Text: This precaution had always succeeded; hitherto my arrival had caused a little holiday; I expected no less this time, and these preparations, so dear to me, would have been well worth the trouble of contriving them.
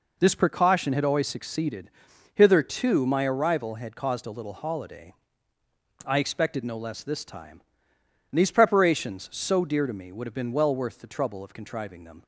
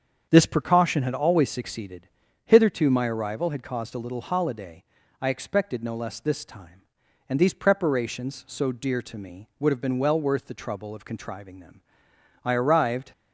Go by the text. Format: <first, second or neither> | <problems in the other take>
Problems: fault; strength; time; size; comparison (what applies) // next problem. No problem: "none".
first | starts louder than the rest; strong; until 1.3 s; 7 dB // goes on to say "I arrived"; noticeable; from 12.4 s on; 0.68 s long